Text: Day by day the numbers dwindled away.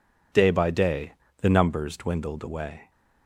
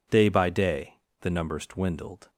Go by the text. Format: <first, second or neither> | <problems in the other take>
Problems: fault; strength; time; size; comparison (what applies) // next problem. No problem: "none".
first | pauses between "day" and "the"; slight; at 0.9 s; 0.26 s long; slight in the first // stops before "away"; at 2.2 s